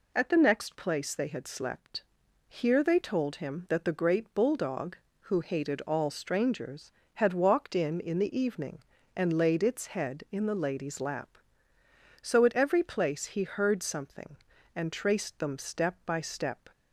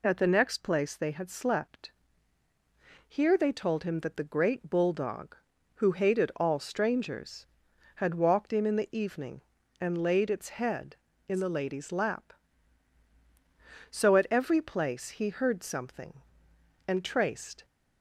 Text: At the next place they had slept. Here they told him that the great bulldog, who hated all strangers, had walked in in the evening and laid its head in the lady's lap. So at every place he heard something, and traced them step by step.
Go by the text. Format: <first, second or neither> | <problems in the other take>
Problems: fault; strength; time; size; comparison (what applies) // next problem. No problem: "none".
first | stops before "them step by step"; at 17.6 s